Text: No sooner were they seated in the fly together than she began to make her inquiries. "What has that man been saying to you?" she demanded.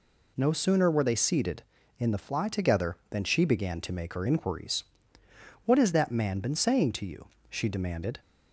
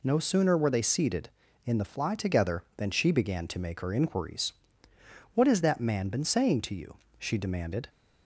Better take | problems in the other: neither | none

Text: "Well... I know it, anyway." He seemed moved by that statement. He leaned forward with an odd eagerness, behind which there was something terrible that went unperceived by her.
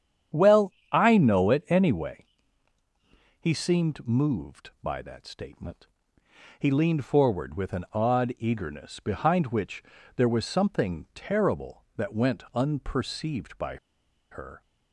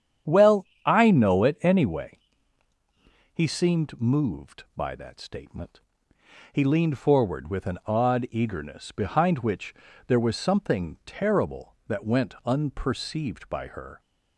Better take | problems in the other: second | starts louder than the rest; strong; until 1.5 s; 9 dB; strong in the second // pauses between "which" and "there"; slight; at 9.8 s; 0.32 s long; slight in the second // pauses between "by" and "her"; noticeable; at 13.7 s; 0.56 s long

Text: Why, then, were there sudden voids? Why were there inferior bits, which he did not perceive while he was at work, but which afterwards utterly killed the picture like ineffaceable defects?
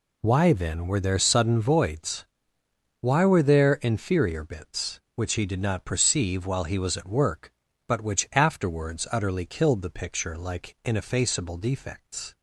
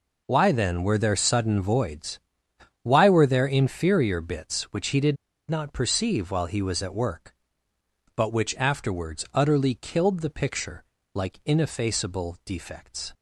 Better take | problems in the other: first | pauses between "did" and "not"; slight; at 5.1 s; 0.34 s long // pauses between "picture" and "like"; slight; at 10.8 s; 0.28 s long

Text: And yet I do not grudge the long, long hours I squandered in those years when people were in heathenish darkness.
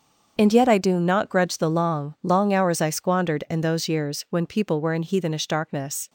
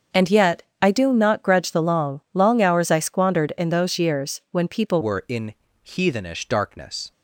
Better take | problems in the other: first | starts louder than the rest; until 1.3 s; 7 dB; also in the first // pauses between "yet" and "I"; slight; at 0.6 s; 0.18 s long // changes voice at "were"; from 5.0 s on; 2.1 s long // pauses between "in" and "heathenish"; slight; at 5.5 s; 0.32 s long

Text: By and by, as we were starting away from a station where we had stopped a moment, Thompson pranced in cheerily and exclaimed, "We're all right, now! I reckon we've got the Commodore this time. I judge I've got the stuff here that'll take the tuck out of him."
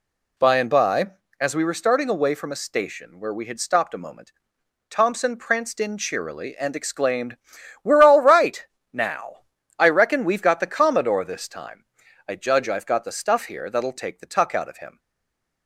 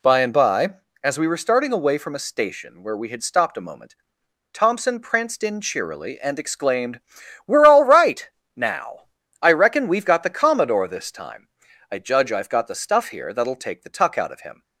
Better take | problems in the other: second | stays silent after the last word; slight; from 14.9 s on; 0.7 s long

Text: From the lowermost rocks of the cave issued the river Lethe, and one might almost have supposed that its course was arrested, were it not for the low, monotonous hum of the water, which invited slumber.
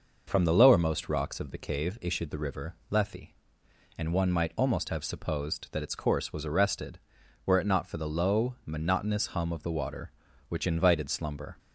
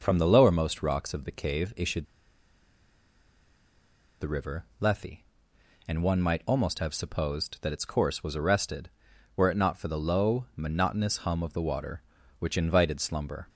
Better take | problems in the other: first | pauses between "issued" and "the"; strong; at 2.0 s; 2.1 s long // pauses between "river" and "Lethe"; slight; at 4.6 s; 0.16 s long; slight in the first

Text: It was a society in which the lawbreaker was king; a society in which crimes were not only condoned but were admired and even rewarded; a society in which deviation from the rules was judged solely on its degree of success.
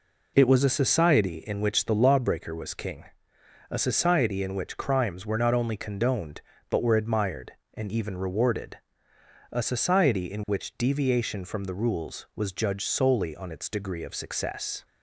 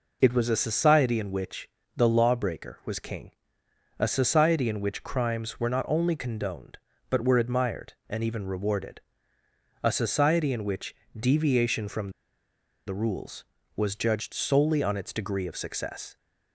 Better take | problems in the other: first | pauses between "which" and "the"; slight; at 1.6 s; 0.26 s long // pauses between "which" and "deviation"; slight; at 10.9 s; 0.20 s long // pauses between "from" and "the"; noticeable; at 12.1 s; 0.74 s long

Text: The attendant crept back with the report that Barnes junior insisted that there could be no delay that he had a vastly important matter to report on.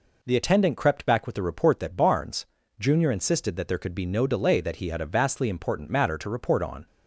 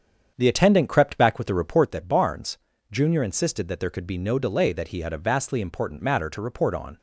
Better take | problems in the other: first | starts louder than the rest; strong; until 1.9 s; 7.5 dB // pauses between "Barnes" and "junior"; slight; at 2.5 s; 0.32 s long; slight in the first

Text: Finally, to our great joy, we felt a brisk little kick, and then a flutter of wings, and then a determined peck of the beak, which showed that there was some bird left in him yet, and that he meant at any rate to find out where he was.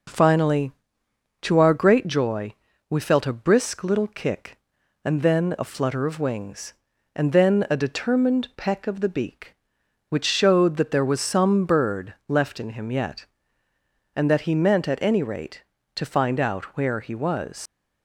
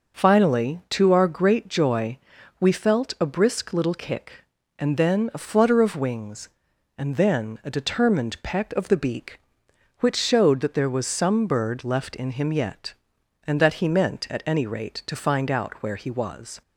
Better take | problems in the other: second | leaves "was" unfinished; at 17.6 s; 105 ms

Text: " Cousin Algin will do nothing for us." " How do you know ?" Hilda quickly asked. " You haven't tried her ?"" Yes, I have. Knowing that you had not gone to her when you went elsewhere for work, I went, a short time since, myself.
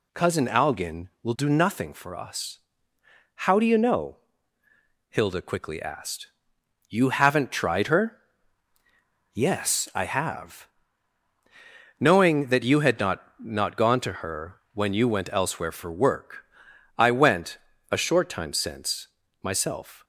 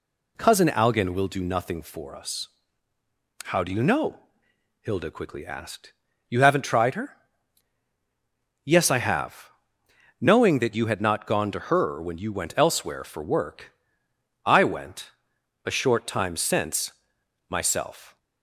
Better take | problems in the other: second | says "not" twice; at 13.3 s

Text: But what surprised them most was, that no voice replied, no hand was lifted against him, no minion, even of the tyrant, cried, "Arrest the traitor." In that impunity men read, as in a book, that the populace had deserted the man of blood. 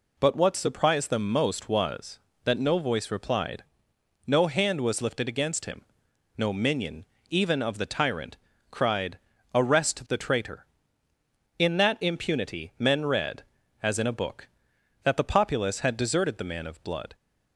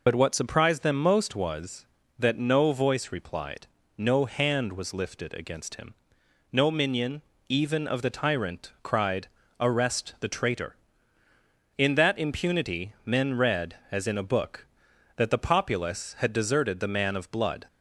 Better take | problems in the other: first | loses the start of "But"; at 0.0 s; 45 ms

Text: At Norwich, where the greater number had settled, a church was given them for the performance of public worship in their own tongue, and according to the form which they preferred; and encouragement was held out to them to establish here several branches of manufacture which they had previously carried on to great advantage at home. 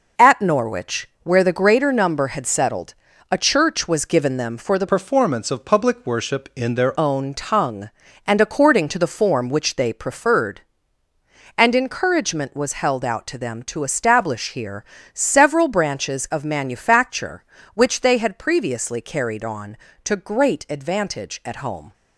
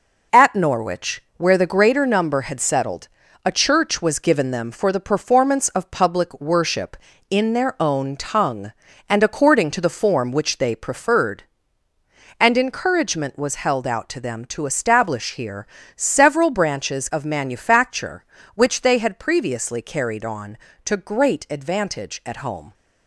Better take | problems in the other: second | changes voice from "performance" to "their"; from 4.8 to 6.9 s; 2.1 s long // pauses between "here" and "several"; slight; at 14.8 s; 0.30 s long; slight in the second

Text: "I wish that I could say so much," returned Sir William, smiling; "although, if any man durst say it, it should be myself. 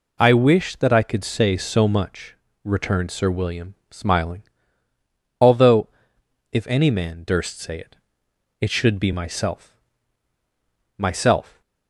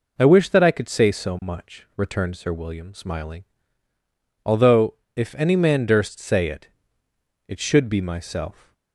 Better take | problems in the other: second | says "myself" twice; at 10.9 s

